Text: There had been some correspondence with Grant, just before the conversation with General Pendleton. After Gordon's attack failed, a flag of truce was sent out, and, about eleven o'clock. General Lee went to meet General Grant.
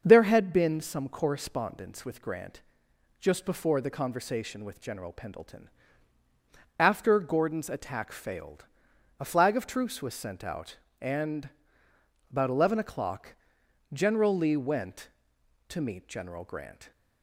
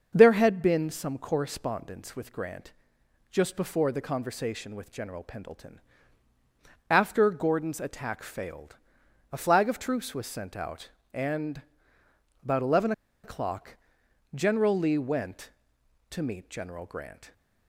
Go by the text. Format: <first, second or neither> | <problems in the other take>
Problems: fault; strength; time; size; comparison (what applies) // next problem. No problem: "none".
first | starts louder than the rest; until 1.1 s; 6.5 dB; also in the first // pauses between "eleven" and "o'clock"; slight; at 12.9 s; 0.32 s long